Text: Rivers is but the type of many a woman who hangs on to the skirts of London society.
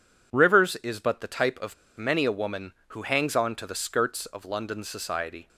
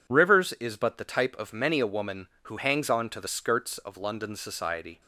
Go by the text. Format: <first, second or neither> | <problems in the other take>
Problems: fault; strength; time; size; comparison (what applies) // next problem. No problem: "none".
second | pauses between "of" and "many"; slight; at 1.7 s; 0.22 s long